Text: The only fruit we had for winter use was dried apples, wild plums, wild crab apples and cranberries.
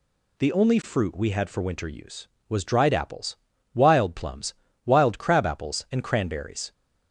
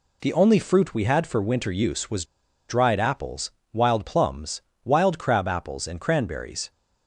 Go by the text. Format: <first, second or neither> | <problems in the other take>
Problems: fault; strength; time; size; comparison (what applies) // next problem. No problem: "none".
first | pauses between "was" and "dried"; at 2.2 s; 0.42 s long